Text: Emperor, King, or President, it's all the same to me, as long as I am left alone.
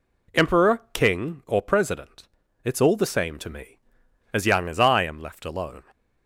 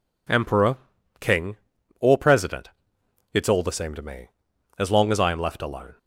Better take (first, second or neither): second